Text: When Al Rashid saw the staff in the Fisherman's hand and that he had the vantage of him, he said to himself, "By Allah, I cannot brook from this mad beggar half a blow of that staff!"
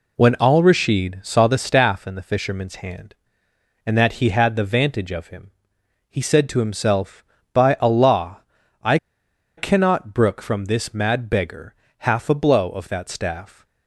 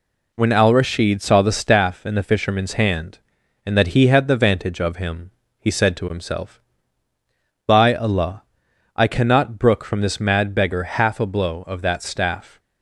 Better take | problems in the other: second | pauses between "I" and "cannot"; noticeable; at 8.9 s; 0.61 s long // pauses between "beggar" and "half"; slight; at 11.7 s; 0.24 s long

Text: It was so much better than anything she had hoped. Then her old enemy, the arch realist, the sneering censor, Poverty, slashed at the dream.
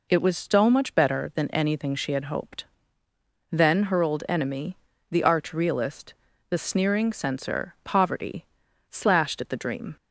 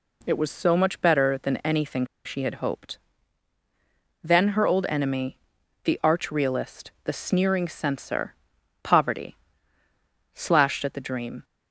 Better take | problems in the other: first | pauses between "anything" and "she"; slight; at 2.0 s; 0.19 s long

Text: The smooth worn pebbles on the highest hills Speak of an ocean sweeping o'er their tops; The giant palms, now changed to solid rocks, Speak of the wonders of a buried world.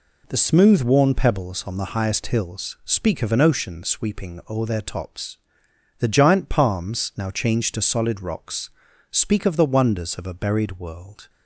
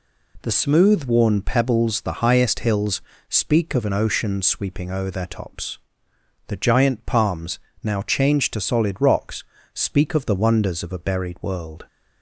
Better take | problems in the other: first | skips "on"; at 2.0 s // pauses between "hills" and "Speak"; slight; at 3.0 s; 0.28 s long

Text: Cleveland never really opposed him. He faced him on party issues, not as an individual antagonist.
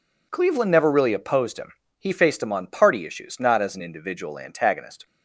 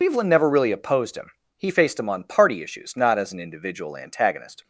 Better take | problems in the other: first | loses the start of "Cleveland"; at 0.0 s; 120 ms

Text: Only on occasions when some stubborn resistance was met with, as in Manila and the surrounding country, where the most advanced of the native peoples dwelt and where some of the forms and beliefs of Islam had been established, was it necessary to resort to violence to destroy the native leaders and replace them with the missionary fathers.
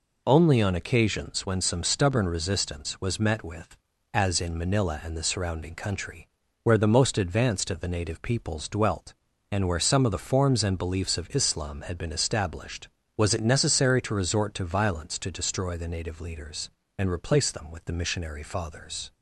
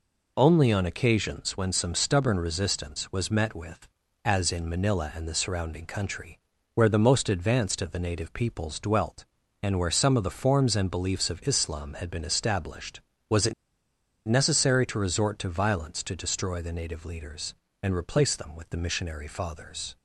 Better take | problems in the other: first | pauses between "it" and "necessary"; noticeable; at 13.5 s; 0.72 s long

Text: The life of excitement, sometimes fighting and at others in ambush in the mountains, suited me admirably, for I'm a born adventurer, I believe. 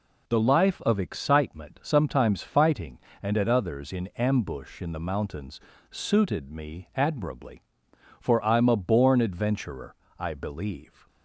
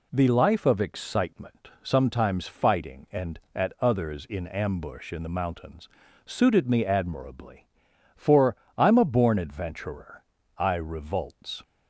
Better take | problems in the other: first | pauses between "for" and "I'm"; slight; at 8.5 s; 0.20 s long // says "revolts" for "believe"; at 10.7 s

